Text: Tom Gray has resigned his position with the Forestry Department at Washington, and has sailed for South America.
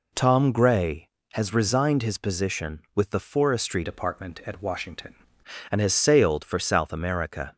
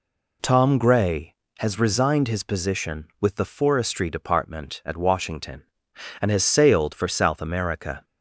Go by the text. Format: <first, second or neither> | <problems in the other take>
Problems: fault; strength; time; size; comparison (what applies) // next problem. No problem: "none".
second | changes voice from "Department" to "Washington"; from 3.8 to 5.1 s; 1.3 s long